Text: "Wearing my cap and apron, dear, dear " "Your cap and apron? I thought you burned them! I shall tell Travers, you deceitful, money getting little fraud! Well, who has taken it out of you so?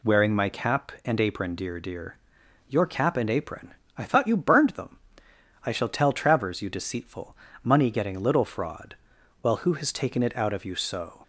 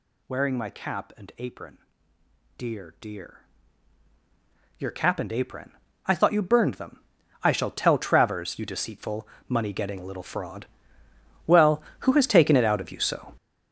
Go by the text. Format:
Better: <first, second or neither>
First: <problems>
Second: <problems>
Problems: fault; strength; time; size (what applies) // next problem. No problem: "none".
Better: first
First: none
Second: gets louder; strong; throughout; 16 dB